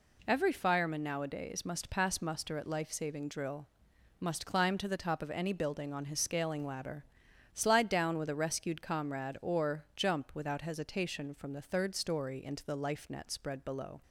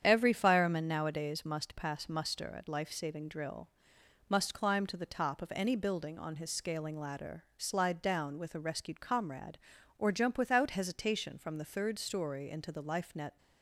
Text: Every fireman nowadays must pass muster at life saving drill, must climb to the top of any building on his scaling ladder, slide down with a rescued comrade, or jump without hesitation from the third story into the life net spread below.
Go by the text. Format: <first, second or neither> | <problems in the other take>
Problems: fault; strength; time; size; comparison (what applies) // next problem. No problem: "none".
first | starts louder than the rest; strong; until 1.0 s; 8.5 dB // stops before "spread below"; at 13.3 s